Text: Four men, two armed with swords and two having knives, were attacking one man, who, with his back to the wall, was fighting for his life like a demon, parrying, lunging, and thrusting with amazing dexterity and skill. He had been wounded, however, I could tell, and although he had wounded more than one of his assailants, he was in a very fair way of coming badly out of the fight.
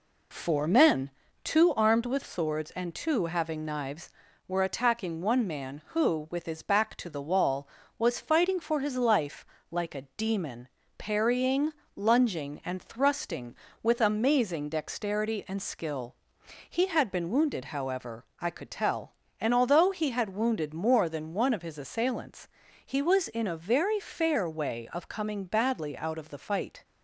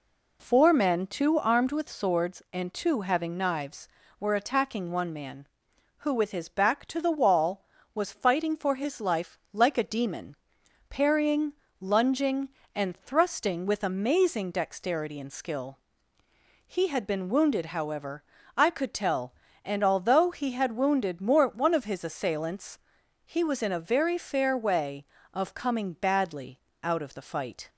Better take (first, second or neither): first